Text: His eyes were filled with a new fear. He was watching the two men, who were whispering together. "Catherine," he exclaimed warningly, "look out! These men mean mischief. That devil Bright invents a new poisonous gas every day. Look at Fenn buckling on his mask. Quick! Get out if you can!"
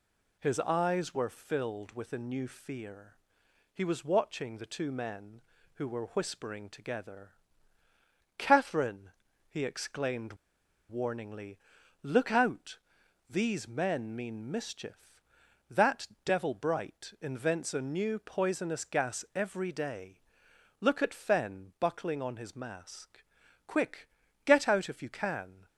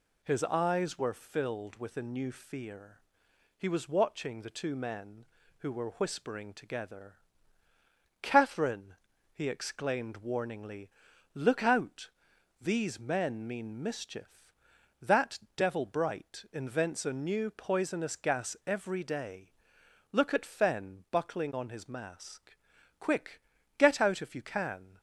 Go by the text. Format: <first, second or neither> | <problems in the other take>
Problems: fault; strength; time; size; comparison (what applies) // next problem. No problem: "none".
second | pauses between "exclaimed" and "warningly"; noticeable; at 10.3 s; 0.55 s long // pauses between "That" and "devil"; slight; at 16.0 s; 0.16 s long; slight in the second